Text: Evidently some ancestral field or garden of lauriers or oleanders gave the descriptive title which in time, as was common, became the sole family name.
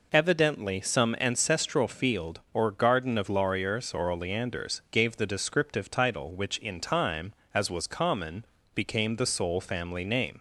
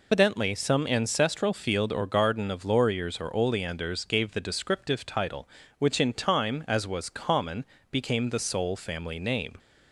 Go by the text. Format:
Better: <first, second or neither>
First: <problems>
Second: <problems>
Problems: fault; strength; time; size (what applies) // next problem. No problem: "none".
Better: first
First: none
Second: loses the start of "Evidently"; at 0.1 s; 155 ms